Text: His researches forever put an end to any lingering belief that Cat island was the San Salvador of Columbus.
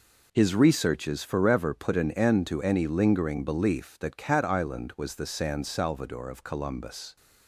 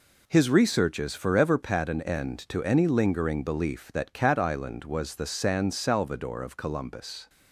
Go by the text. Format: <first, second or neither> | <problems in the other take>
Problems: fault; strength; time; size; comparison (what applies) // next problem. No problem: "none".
first | says "pat" for "put"; at 1.5 s